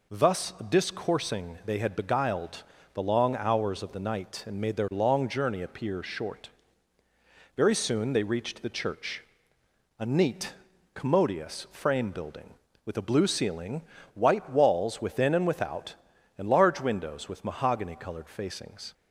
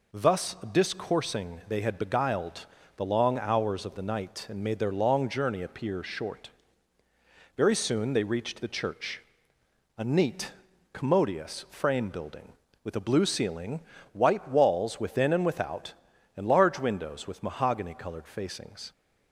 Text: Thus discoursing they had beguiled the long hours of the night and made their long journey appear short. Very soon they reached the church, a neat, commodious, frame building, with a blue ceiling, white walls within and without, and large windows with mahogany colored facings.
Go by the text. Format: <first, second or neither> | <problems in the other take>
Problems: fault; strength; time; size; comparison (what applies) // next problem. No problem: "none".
neither | pauses between "Thus" and "discoursing"; slight; the same in both // pauses between "beguiled" and "the"; slight; the same in both